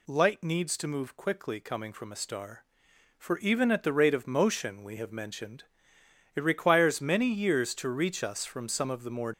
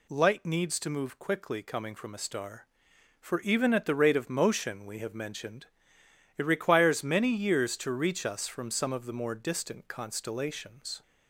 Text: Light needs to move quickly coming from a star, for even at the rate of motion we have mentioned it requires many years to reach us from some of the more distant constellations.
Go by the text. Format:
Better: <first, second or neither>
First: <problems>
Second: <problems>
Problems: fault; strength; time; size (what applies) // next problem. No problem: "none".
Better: second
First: pauses between "mentioned" and "it"; noticeable; at 5.6 s; 0.72 s long // stops before "distant constellations"; at 9.3 s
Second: pauses between "mentioned" and "it"; noticeable; at 5.6 s; 0.72 s long